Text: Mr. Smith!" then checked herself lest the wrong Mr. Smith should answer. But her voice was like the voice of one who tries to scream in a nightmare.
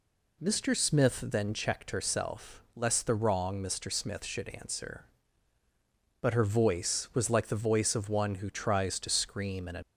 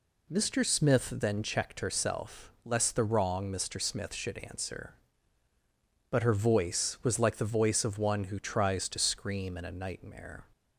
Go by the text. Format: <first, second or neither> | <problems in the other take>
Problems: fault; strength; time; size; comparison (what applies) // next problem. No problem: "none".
second | stops before "nightmare"; at 9.8 s